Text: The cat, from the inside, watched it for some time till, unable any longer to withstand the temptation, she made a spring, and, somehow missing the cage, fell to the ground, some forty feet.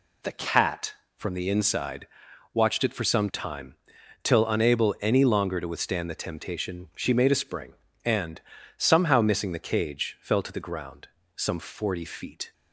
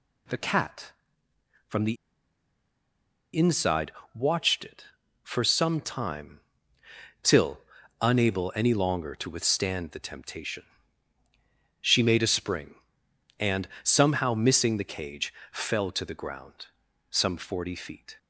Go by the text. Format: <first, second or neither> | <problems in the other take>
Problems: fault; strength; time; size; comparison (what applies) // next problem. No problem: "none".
first | pauses between "the" and "inside"; strong; at 1.9 s; 1.4 s long // pauses between "time" and "till"; noticeable; at 6.3 s; 0.82 s long; noticeable in the first